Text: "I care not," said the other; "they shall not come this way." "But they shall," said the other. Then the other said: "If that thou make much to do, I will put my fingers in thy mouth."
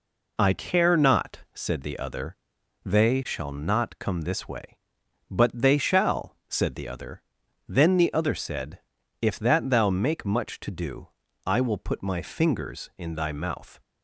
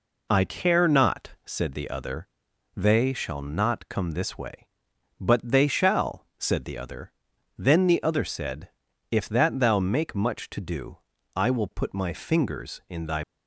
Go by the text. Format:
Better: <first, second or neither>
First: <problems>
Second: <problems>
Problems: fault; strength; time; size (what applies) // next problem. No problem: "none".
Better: first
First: none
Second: stops before "mouth"; at 13.2 s